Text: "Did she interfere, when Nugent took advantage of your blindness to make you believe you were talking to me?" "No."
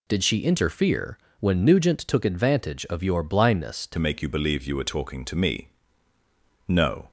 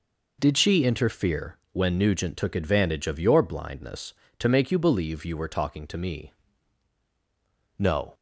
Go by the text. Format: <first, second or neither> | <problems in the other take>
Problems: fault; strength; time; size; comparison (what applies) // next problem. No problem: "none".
second | changes voice at "make"; from 3.9 s on; 3.2 s long